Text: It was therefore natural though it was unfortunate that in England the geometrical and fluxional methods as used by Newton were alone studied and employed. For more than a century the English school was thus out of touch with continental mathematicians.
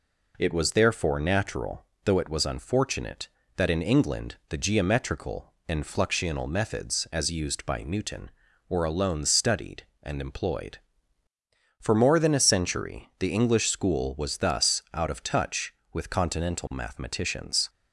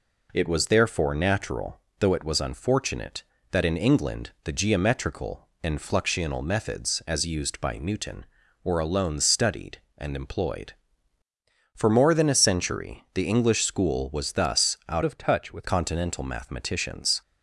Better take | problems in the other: first | pauses between "natural" and "though"; slight; at 1.7 s; 0.20 s long; slight in the first // changes voice from "of" to "with"; from 15.0 to 15.6 s; 0.6 s long

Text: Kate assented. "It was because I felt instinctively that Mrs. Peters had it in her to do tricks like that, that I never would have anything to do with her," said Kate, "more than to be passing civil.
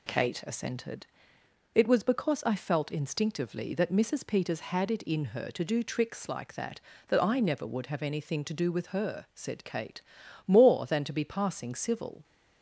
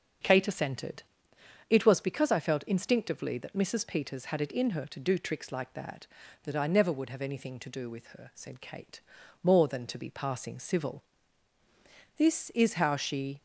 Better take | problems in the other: first | starts louder than the rest; until 1.8 s; 6.5 dB // goes on to say "This is how she"; noticeable; from 12.1 s on; 1.2 s long

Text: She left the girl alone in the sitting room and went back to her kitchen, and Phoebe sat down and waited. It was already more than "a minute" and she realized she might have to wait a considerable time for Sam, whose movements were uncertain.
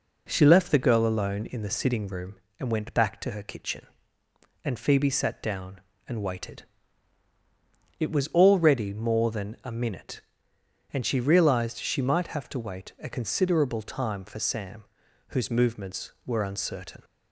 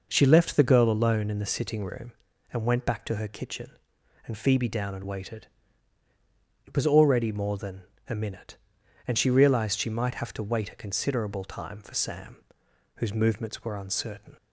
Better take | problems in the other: first | skips "sat"; at 4.6 s // pauses between "than" and "a"; slight; at 7.8 s; 0.26 s long

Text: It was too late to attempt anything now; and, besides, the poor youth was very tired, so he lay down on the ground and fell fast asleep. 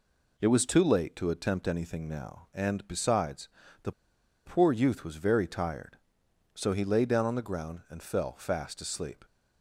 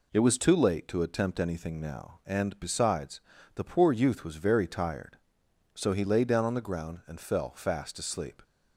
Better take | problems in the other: second | pauses between "the" and "poor"; noticeable; at 3.9 s; 0.54 s long

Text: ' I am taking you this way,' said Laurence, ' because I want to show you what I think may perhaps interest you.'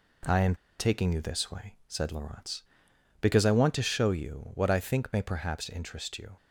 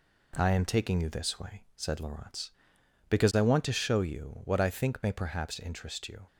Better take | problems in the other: second | pauses between "am" and "taking"; slight; at 0.5 s; 0.24 s long

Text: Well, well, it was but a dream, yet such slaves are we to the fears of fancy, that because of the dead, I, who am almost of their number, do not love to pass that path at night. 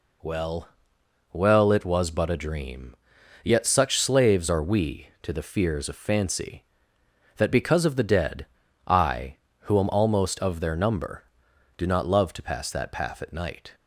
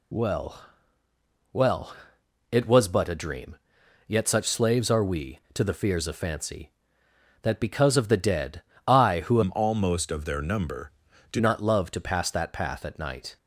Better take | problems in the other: first | changes voice from "am" to "do"; from 9.4 to 11.3 s; 1.9 s long

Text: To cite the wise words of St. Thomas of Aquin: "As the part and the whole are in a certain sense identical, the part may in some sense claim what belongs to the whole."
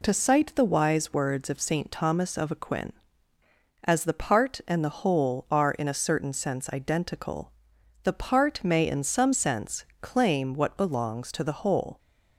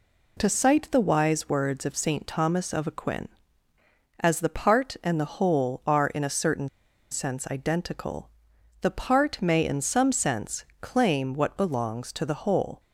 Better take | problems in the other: first | pauses between "certain" and "sense"; at 6.6 s; 0.43 s long // pauses between "sense" and "claim"; slight; at 10.6 s; 0.16 s long; slight in the first

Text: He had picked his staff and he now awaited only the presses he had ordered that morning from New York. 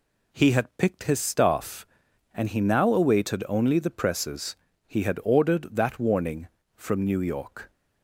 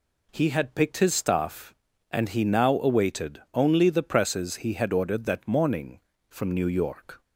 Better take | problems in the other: second | pauses between "presses" and "he"; slight; at 4.5 s; 0.30 s long // says "warning" for "morning"; at 5.9 s

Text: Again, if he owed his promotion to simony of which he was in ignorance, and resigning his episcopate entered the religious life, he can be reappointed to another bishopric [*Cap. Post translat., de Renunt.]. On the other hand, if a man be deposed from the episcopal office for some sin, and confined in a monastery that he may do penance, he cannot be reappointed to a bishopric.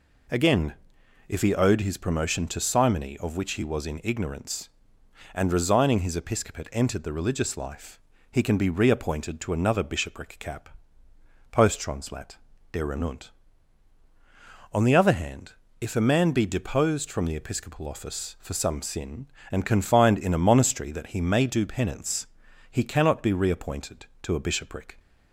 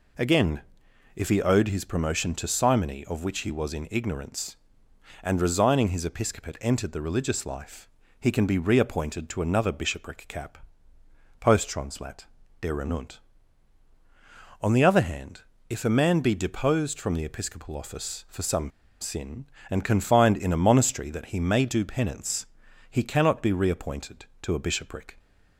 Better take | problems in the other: first | pauses between "some" and "sin"; slight; at 18.6 s; 0.31 s long

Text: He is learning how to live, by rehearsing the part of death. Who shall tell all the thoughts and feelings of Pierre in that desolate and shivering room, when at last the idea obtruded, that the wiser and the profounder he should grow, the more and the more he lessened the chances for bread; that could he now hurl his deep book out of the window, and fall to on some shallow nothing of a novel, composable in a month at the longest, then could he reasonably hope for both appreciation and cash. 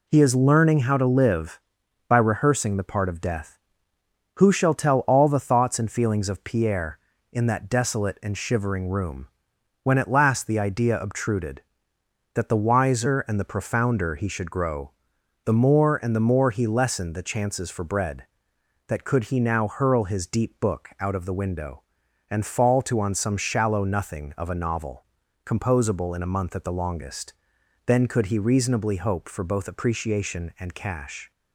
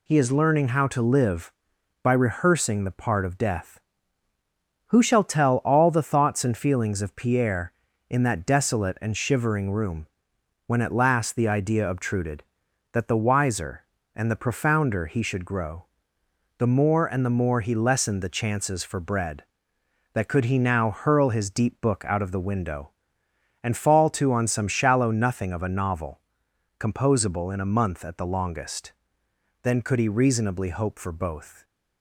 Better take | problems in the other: first | stops before "appreciation and cash"; at 31.6 s

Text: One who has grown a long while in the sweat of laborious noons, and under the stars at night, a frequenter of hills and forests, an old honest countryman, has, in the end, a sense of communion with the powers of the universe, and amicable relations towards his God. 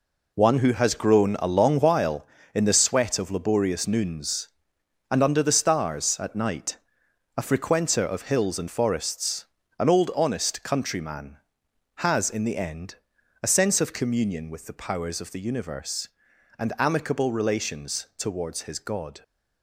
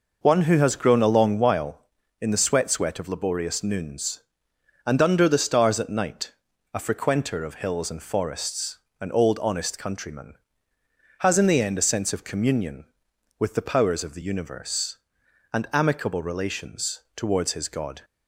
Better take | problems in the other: first | says "sweat" twice; at 2.7 s

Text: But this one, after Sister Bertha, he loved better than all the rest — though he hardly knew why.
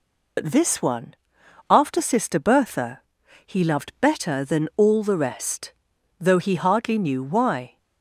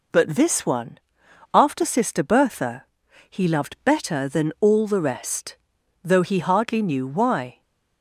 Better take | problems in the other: second | loses the start of "But"; at 0.3 s; 95 ms

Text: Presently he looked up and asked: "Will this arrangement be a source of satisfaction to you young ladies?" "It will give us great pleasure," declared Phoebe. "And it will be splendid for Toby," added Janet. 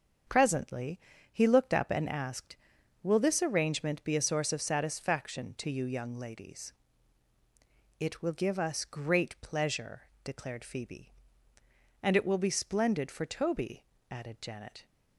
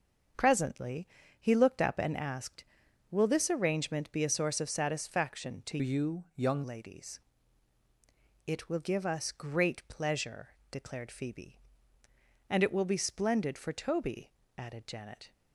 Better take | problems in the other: first | starts louder than the rest; until 1.6 s; 6.5 dB; also in the first // pauses between "Presently" and "he"; slight; at 1.0 s; 0.32 s long; slight in the first // changes voice from "you" to "young"; from 5.7 to 6.6 s; 0.9 s long

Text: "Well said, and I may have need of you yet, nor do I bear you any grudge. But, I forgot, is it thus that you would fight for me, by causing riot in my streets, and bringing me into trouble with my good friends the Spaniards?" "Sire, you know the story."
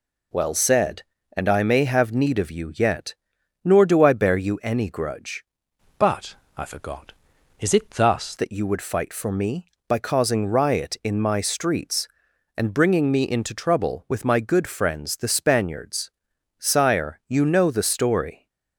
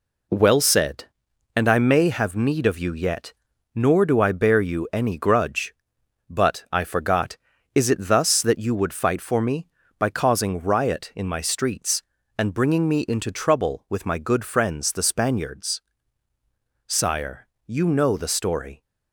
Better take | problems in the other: second | changes voice from "But" to "thus"; from 5.9 to 8.3 s; 2.4 s long

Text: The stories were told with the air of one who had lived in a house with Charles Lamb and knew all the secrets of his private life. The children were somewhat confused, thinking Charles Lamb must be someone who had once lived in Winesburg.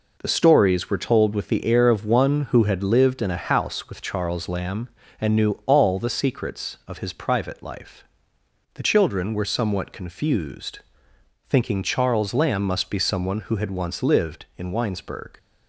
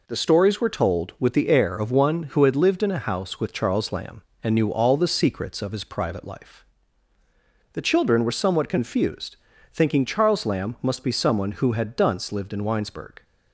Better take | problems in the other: first | says "dunce" for "once"; at 11.9 s

